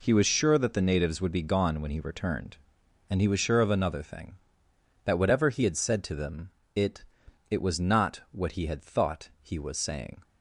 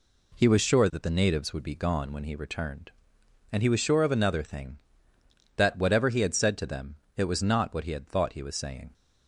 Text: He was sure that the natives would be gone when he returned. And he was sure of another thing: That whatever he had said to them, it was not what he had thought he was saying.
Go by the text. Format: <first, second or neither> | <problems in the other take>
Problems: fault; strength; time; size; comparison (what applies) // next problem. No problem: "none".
second | says "it" twice; at 7.4 s